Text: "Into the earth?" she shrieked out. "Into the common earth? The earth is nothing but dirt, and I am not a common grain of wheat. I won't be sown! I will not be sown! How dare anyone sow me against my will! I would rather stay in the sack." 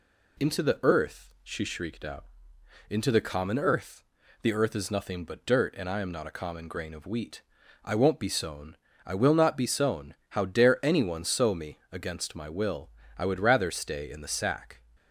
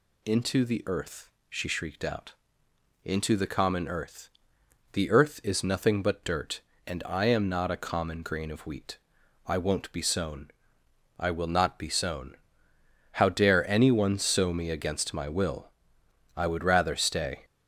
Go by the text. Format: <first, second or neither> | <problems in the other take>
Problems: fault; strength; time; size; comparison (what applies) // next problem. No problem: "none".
first | stops before "in the sack"; at 17.4 s